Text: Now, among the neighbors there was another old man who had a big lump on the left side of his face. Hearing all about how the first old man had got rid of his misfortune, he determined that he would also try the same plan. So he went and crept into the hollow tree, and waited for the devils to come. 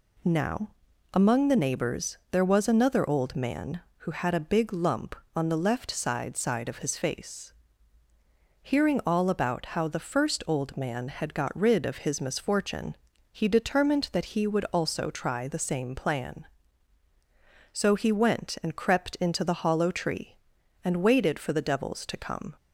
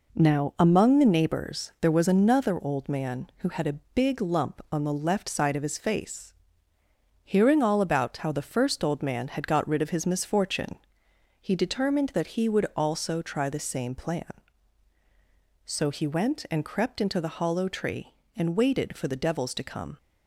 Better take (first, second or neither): second